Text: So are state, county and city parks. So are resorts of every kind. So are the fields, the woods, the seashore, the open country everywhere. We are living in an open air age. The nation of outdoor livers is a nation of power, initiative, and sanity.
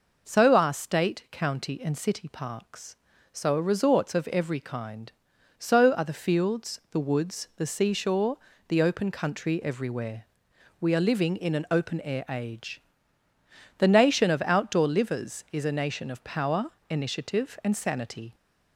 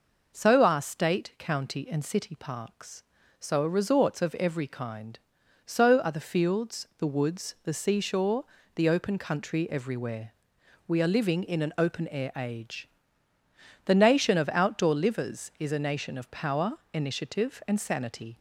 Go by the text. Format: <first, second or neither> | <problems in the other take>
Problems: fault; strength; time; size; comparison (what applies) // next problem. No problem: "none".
neither | none